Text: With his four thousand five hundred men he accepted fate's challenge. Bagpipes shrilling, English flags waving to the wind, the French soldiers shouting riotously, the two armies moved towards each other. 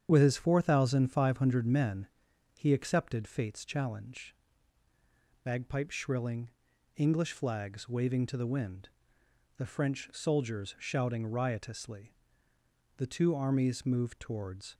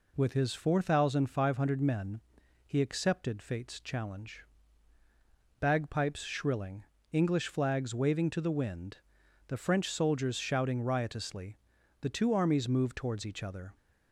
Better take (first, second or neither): second